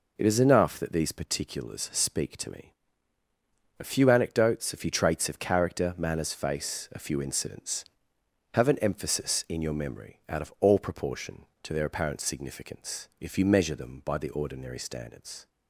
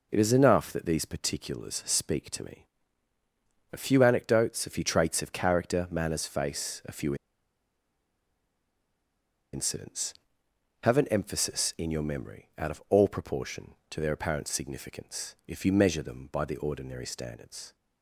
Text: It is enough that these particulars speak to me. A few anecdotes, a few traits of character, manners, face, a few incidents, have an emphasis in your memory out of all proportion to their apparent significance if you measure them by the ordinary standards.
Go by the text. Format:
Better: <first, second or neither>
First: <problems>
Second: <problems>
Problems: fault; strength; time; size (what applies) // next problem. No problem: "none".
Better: first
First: none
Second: pauses between "few" and "incidents"; strong; at 7.1 s; 2.3 s long